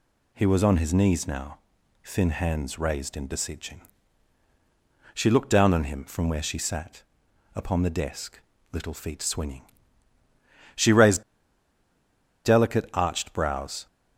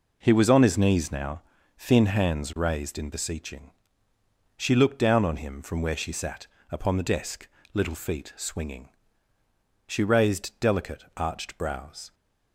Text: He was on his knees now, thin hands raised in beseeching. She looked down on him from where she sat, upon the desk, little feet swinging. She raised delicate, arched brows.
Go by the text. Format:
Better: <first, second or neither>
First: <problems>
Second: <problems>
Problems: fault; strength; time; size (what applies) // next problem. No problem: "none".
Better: second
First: pauses between "raised" and "delicate"; at 11.2 s; 1.2 s long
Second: none